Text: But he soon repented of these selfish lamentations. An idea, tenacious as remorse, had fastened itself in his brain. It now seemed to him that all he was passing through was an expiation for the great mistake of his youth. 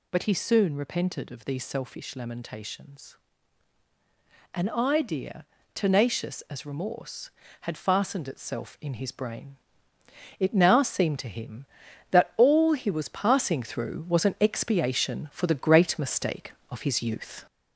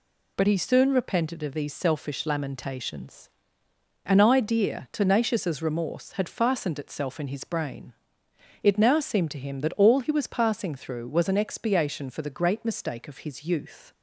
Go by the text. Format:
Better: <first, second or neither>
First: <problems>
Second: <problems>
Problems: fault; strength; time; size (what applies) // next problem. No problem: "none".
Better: second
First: gets louder; noticeable; throughout; 4.5 dB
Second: none